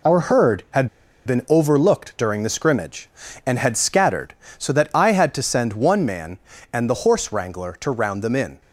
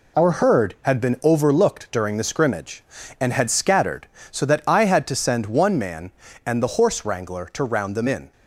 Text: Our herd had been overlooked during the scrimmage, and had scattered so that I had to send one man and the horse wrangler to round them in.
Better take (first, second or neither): second